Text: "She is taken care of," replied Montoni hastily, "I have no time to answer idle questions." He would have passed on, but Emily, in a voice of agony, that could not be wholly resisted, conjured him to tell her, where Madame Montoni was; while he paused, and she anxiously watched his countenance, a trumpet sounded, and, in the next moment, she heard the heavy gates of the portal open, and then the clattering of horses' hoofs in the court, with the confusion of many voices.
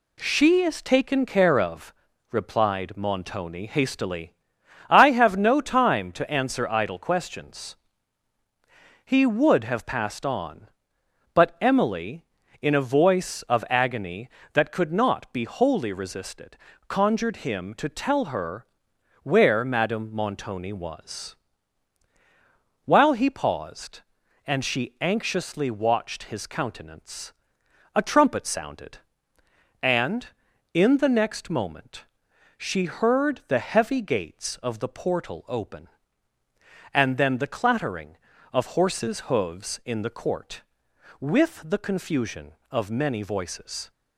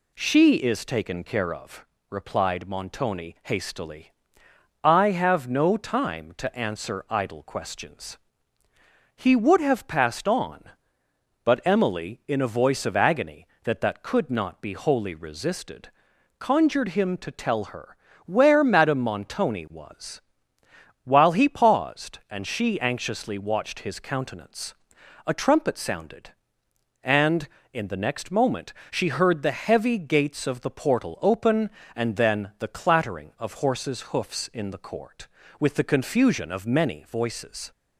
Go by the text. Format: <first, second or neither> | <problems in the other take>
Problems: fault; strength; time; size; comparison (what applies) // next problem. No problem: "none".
first | says "that" twice; at 13.8 s